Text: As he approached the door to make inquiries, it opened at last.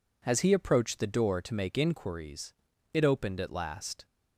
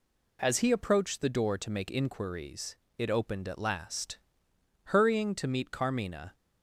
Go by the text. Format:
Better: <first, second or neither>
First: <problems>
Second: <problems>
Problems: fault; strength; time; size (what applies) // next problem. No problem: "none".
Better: first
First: none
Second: goes on to say "Hurrying to meet Carmina"; from 4.8 s on; 1.4 s long